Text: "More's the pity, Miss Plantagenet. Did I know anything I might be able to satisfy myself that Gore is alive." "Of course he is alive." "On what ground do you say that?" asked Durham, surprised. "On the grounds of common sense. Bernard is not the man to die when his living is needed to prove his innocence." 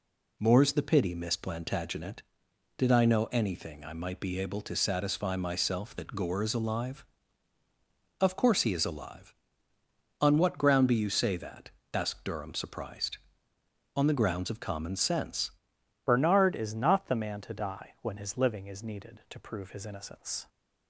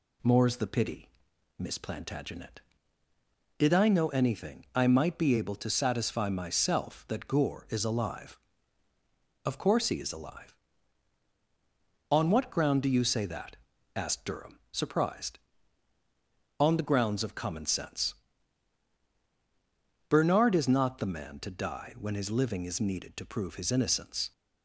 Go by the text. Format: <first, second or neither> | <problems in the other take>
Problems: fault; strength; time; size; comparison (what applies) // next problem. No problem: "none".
second | changes voice at "Bernard"; from 16.0 s on; 4.4 s long